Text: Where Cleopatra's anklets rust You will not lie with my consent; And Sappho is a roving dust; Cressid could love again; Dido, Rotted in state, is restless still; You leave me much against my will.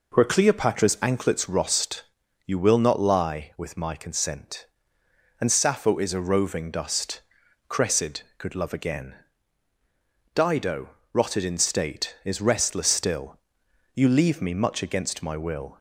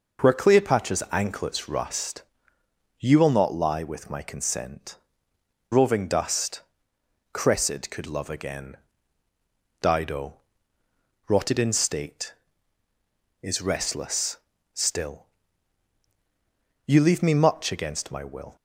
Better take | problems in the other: first | pauses between "rust" and "You"; noticeable; at 2.2 s; 0.76 s long; also in the first // skips "And Sappho is a"; at 5.3 s // pauses between "restless" and "still"; slight; at 14.3 s; 0.36 s long

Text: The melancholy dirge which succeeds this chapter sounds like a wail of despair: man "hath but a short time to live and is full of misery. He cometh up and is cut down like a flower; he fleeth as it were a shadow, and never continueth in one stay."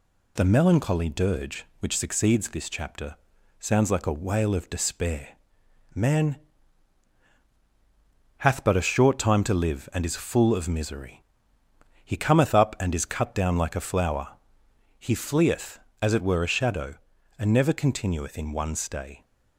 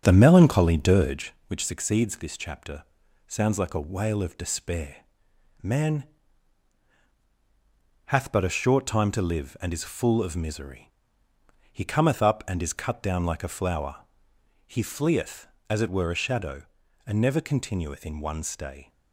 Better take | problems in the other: first | starts louder than the rest; strong; until 1.3 s; 7.5 dB // pauses between "chapter" and "sounds"; at 2.8 s; 0.42 s long; also in the first // pauses between "man" and "hath"; strong; at 6.0 s; 2.0 s long; strong in the first

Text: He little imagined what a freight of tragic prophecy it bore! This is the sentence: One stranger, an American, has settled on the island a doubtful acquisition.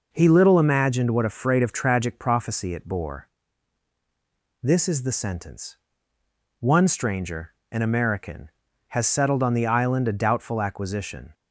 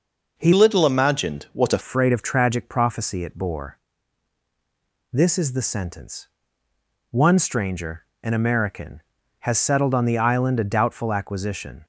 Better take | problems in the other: first | changes voice from "little" to "a"; from 0.5 to 1.7 s; 1.2 s long

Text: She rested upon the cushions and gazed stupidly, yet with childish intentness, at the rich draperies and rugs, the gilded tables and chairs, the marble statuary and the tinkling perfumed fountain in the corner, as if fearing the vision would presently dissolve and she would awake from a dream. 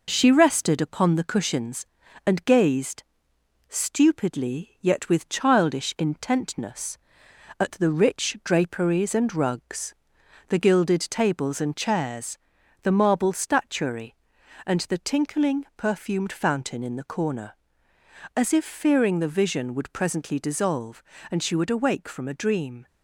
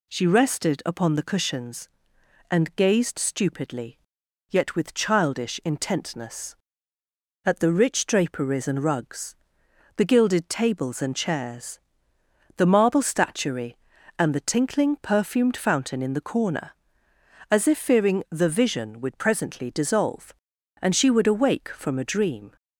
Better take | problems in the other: second | gets quieter; slight; throughout; 2 dB // pauses between "gazed" and "stupidly"; noticeable; at 3.0 s; 0.66 s long

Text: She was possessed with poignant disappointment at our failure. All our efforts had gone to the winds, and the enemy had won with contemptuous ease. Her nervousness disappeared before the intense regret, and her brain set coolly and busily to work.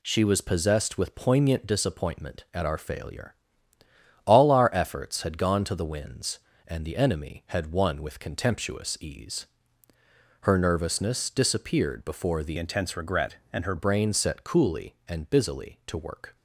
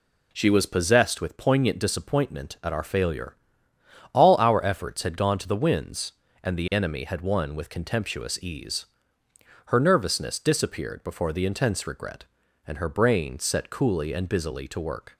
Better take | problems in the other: second | changes voice from "intense" to "her"; from 12.5 to 13.7 s; 1.2 s long

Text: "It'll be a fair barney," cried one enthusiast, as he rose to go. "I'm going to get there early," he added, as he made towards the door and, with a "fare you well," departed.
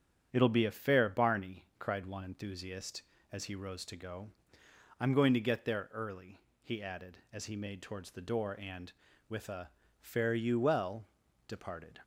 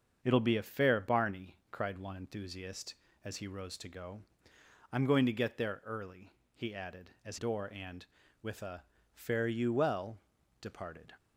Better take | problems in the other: first | starts louder than the rest; until 1.2 s; 7 dB; strong in the first // skips "he made towards the"; at 7.3 s // pauses between "a" and "fare"; slight; at 8.8 s; 0.28 s long; slight in the first

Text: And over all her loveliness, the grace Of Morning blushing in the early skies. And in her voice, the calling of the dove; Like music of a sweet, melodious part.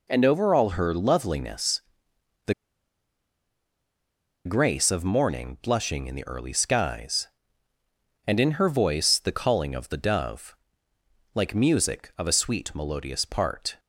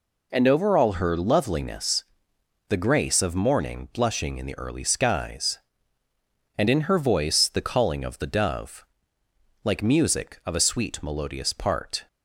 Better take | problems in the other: second | pauses between "the" and "grace"; strong; at 2.5 s; 1.9 s long

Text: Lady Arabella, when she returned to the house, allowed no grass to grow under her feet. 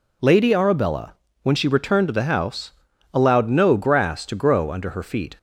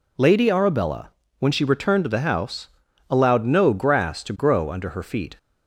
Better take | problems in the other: neither | none

